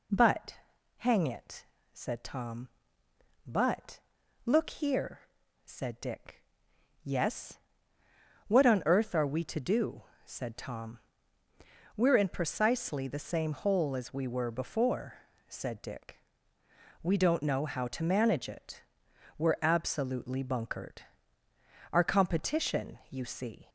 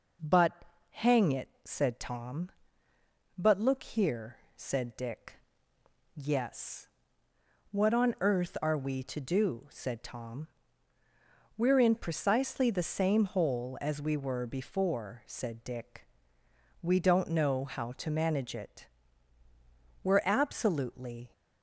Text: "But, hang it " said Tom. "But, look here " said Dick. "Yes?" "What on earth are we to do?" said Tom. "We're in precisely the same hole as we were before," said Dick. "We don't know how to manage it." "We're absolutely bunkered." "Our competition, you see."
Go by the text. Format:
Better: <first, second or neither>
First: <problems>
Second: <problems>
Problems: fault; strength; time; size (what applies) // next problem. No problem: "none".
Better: first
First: none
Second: stops before "bunkered Our competition you see"; at 21.3 s